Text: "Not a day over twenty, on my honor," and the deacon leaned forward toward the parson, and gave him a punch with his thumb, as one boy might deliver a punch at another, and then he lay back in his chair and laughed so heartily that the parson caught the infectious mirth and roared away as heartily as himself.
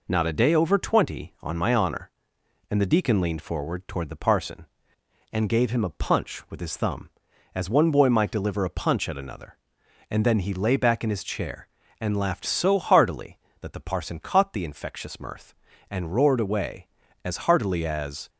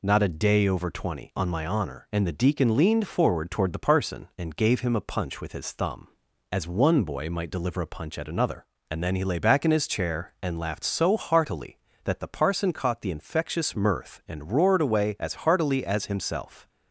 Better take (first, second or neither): second